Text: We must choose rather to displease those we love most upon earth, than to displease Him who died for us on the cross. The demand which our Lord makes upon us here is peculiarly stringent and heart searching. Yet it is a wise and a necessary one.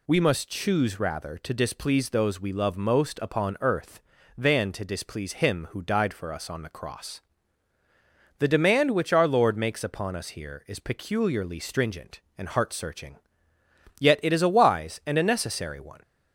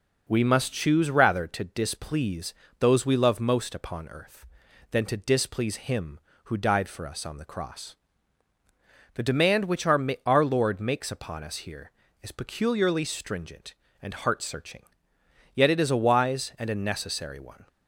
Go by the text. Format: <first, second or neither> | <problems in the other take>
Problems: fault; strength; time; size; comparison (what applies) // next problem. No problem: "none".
first | pauses between "displease" and "those"; slight; at 2.5 s; 0.26 s long // says "our" twice; at 10.2 s